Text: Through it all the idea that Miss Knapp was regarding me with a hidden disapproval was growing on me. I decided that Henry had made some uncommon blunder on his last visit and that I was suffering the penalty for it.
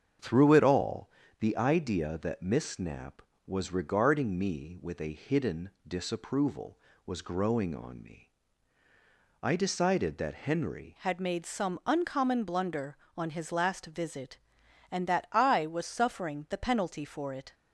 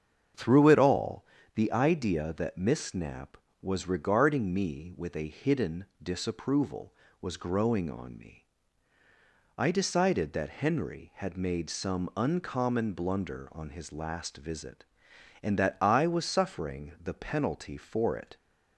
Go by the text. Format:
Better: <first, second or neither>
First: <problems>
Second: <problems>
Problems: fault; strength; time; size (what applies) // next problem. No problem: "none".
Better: second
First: starts louder than the rest; strong; until 1.4 s; 7.5 dB // pauses between "all" and "the"; slight; at 1.1 s; 0.28 s long // pauses between "hidden" and "disapproval"; slight; at 5.7 s; 0.18 s long // changes voice at "had"; from 10.9 s on; 6.6 s long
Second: starts louder than the rest; strong; until 1.6 s; 7.5 dB // pauses between "all" and "the"; slight; at 1.2 s; 0.28 s long // pauses between "hidden" and "disapproval"; slight; at 5.8 s; 0.18 s long